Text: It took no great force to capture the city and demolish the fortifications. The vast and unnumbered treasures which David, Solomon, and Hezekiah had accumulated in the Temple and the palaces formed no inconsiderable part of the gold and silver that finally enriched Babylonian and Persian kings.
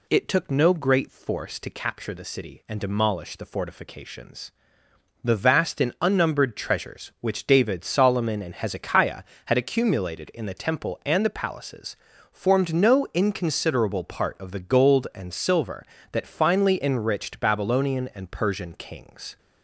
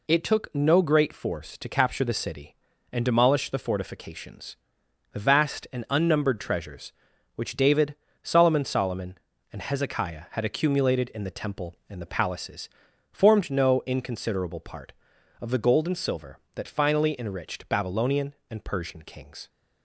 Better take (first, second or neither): first